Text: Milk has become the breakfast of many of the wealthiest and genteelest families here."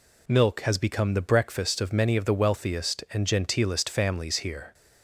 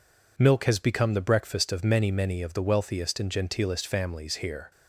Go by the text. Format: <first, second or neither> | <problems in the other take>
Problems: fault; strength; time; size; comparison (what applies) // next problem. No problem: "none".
first | says "many" twice; at 2.1 s